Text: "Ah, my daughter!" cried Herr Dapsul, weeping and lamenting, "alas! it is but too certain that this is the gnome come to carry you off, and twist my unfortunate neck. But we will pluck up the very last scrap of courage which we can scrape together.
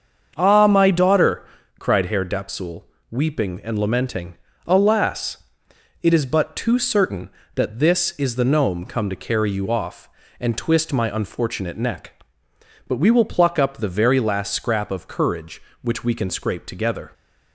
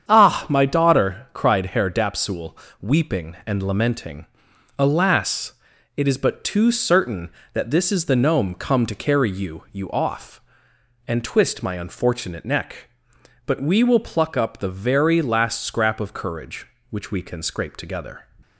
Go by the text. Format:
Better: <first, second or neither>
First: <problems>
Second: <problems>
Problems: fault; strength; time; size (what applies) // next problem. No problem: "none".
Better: first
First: starts louder than the rest; until 1.3 s; 7 dB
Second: starts louder than the rest; strong; until 1.1 s; 8 dB // says "you" twice; at 9.7 s